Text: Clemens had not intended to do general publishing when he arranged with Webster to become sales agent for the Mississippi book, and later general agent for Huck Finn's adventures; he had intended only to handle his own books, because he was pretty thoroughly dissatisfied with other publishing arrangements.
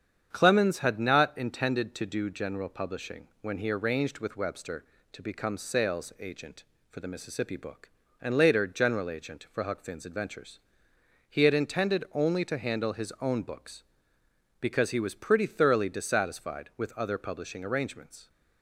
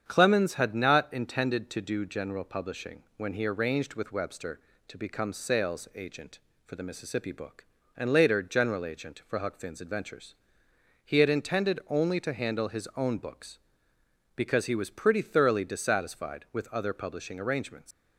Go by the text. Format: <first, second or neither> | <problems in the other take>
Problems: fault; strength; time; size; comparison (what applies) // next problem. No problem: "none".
first | starts louder than the rest; strong; until 1.0 s; 8 dB; strong in the first // leaves "arrangements" unfinished; at 17.9 s; 140 ms